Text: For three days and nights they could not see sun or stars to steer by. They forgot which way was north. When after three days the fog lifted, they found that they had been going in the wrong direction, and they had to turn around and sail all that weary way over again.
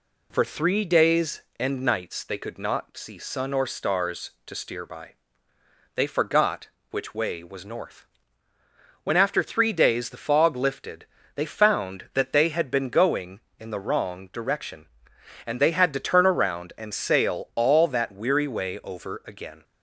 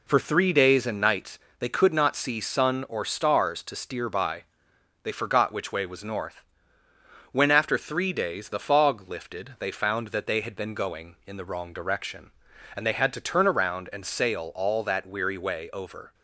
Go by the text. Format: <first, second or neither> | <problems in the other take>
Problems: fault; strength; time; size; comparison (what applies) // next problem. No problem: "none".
first | pauses between "nights" and "they"; slight; at 1.3 s; 0.22 s long // stops before "again"; at 16.1 s